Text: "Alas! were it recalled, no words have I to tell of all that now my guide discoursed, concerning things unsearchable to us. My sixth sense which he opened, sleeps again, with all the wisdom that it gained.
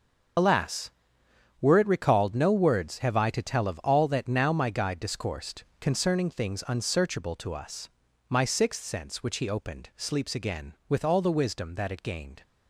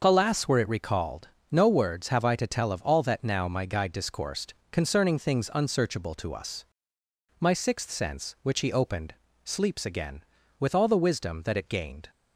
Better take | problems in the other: second | loses the start of "Alas"; at 0.3 s; 65 ms // starts louder than the rest; noticeable; until 2.0 s; 6 dB

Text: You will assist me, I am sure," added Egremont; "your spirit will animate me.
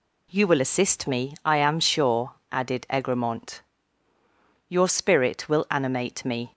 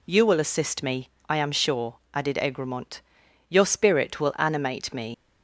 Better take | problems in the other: first | leaves "me" unfinished; at 5.1 s; 85 ms

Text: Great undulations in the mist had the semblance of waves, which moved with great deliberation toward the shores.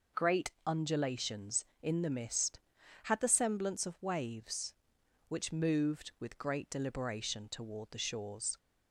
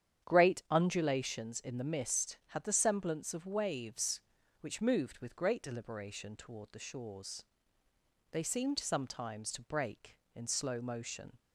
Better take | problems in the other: first | starts louder than the rest; strong; until 1.3 s; 9.5 dB // goes on to say "They seemed sometimes to break in slow motion"; strong; from 8.3 s on; 3.0 s long

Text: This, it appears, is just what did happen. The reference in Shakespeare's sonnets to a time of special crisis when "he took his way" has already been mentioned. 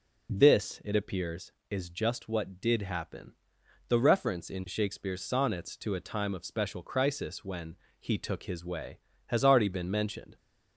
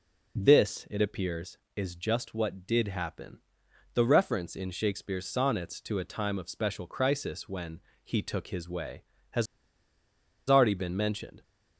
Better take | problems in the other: first | pauses between "when" and "he"; slight; at 7.8 s; 0.24 s long; slight in the first // pauses between "has" and "already"; at 9.4 s; 1.0 s long

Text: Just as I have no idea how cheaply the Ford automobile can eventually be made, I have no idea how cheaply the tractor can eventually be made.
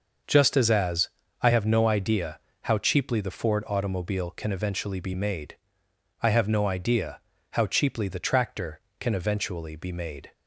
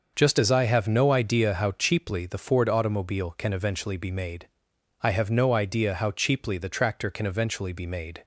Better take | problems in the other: second | starts louder than the rest; until 1.5 s; 6 dB; also in the second // says "as" twice; at 0.6 s // pauses between "idea" and "how"; slight; at 2.3 s; 0.24 s long // pauses between "idea" and "how"; slight; at 7.2 s; 0.30 s long

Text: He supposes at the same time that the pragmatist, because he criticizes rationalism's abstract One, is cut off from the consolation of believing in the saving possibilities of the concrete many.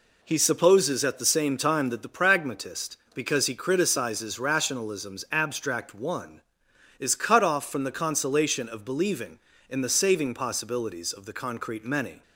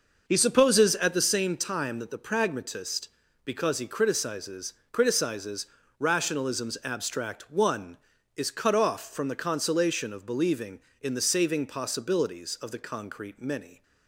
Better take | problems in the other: first | says "criticizes" twice; at 4.9 s

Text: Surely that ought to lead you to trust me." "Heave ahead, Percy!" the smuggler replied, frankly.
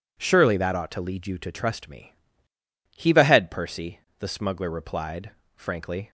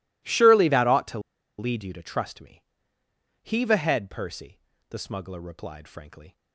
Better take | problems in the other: first | pauses between "to" and "lead"; at 1.1 s; 0.38 s long

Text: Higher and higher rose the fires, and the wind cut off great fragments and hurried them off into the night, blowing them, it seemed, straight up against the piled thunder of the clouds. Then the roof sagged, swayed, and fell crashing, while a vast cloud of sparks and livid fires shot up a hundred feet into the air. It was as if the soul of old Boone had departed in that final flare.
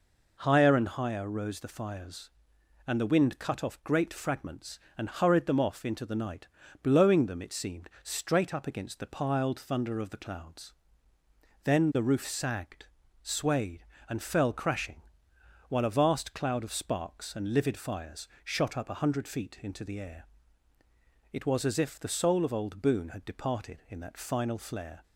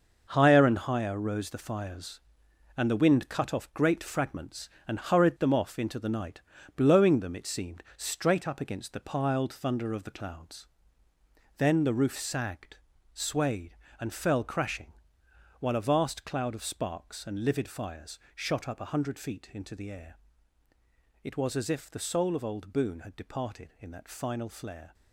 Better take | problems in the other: first | gets quieter; strong; throughout; 9 dB // pauses between "fires" and "shot"; slight; at 18.1 s; 0.16 s long; slight in the first

